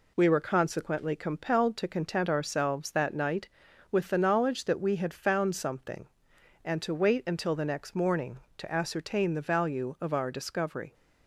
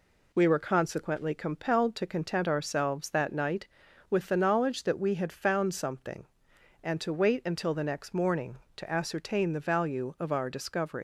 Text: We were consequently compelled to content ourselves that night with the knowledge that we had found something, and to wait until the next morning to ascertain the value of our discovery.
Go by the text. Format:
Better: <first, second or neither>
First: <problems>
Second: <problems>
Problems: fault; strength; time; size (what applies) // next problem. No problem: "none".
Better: first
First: none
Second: leaves "discovery" unfinished; at 10.9 s; 95 ms